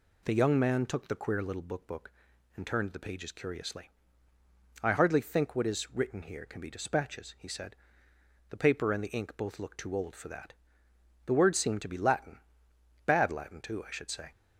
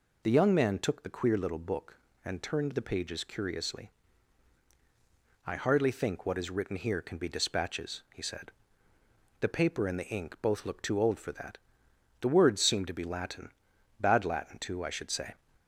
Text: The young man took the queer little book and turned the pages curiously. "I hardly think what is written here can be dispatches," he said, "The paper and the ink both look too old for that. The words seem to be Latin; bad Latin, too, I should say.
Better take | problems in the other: second | says "book" twice; at 1.8 s

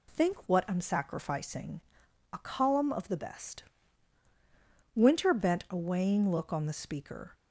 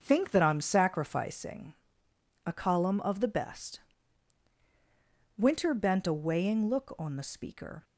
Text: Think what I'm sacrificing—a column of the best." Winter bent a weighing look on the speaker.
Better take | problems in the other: first | starts louder than the rest; until 1.0 s; 6.5 dB // says "that" for "what"; at 0.3 s

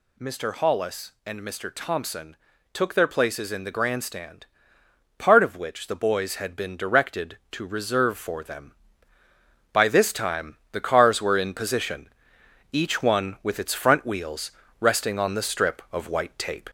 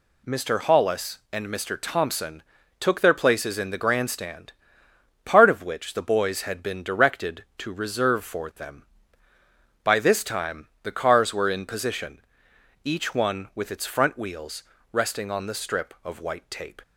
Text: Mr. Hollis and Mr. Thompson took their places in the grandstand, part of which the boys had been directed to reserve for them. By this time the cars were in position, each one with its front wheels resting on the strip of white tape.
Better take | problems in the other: second | gets louder; slight; throughout; 2.5 dB // pauses between "Thompson" and "took"; slight; at 2.3 s; 0.36 s long; slight in the second // pauses between "time" and "the"; slight; at 10.5 s; 0.16 s long; slight in the second // pauses between "wheels" and "resting"; slight; at 14.5 s; 0.28 s long; slight in the second

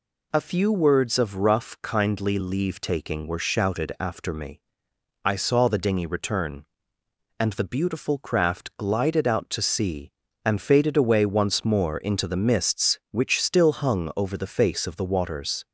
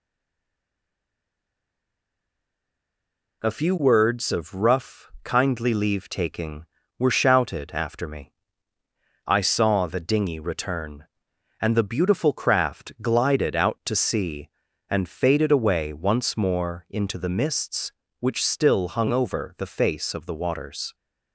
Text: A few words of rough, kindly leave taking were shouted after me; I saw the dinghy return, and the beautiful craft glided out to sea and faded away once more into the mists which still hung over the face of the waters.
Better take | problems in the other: first | stays silent before the first word; strong; until 3.4 s; 3.4 s long

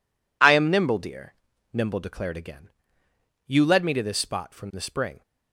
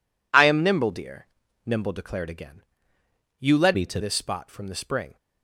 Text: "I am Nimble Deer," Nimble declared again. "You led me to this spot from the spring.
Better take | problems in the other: first | changes voice from "me" to "to"; from 3.7 to 4.0 s; 0.3 s long

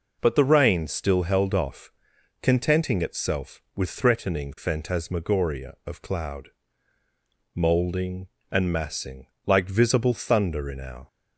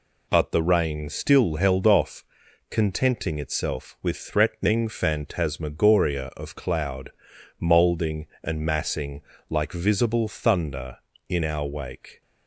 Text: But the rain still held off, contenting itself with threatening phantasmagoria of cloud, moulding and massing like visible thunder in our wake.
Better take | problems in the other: second | pauses between "massing" and "like"; slight; at 9.2 s; 0.18 s long; slight in the second // stops before "wake"; at 11.0 s

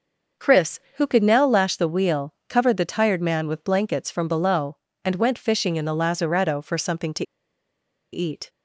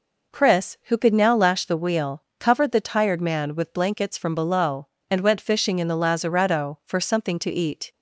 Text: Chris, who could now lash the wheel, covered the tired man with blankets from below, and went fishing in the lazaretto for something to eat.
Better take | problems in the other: second | starts louder than the rest; until 1.5 s; 6 dB // pauses between "to" and "eat"; noticeable; at 7.2 s; 0.88 s long

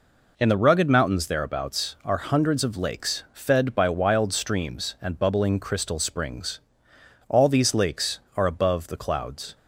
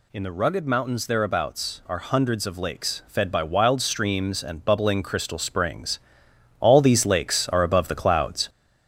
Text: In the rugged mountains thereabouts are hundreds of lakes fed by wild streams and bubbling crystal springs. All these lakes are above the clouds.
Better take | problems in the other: first | gets louder; noticeable; throughout; 5.5 dB

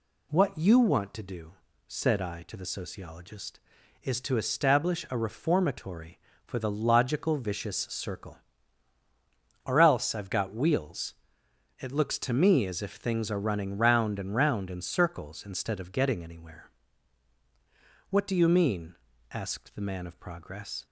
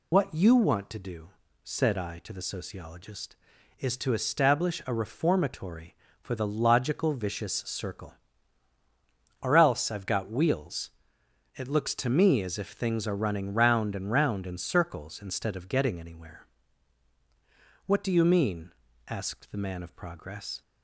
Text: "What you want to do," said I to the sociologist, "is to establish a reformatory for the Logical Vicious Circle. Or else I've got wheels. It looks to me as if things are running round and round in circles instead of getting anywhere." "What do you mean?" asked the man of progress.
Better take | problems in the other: first | loses the start of "What"; at 0.1 s; 50 ms

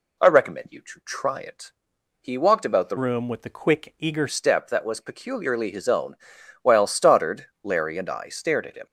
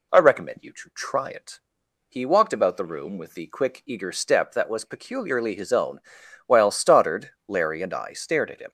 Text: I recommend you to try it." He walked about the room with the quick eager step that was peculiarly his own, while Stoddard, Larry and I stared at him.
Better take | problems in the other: second | changes voice from "room" to "eager"; from 2.9 to 4.2 s; 1.3 s long

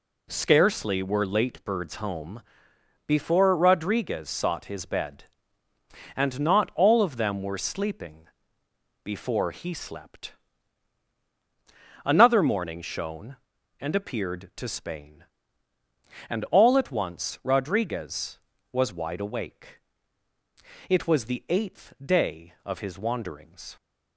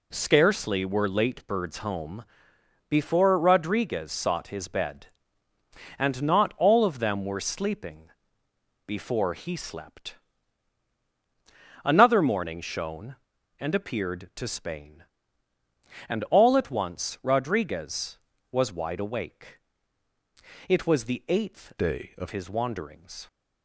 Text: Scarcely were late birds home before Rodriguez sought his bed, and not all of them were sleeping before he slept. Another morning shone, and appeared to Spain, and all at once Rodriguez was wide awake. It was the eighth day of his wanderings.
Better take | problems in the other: first | pauses between "home" and "before"; noticeable; at 2.2 s; 0.64 s long; noticeable in the first // pauses between "sleeping" and "before"; noticeable; at 8.0 s; 0.76 s long; noticeable in the first // changes voice from "day" to "of"; from 21.7 to 22.2 s; 0.5 s long

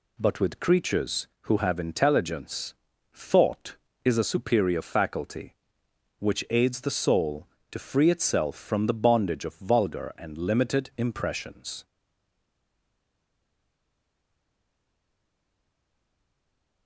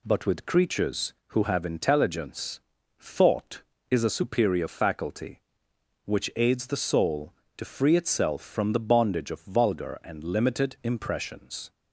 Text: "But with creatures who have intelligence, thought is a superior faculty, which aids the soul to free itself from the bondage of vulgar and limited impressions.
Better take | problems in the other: second | stays silent after the last word; strong; from 11.8 s on; 5.0 s long

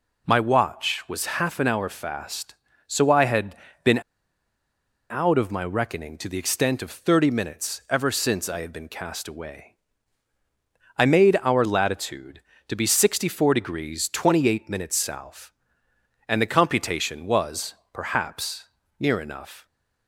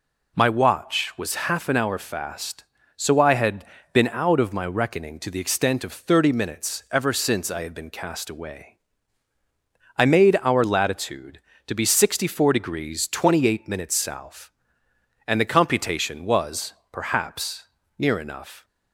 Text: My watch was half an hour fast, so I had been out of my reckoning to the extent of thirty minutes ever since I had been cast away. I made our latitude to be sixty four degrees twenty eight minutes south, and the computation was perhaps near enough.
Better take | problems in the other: second | pauses between "had" and "been"; slight; at 3.5 s; 0.30 s long; slight in the second // pauses between "been" and "out"; at 4.0 s; 1.1 s long // pauses between "was" and "perhaps"; slight; at 17.7 s; 0.18 s long; slight in the second // pauses between "perhaps" and "near"; slight; at 18.6 s; 0.32 s long; slight in the second

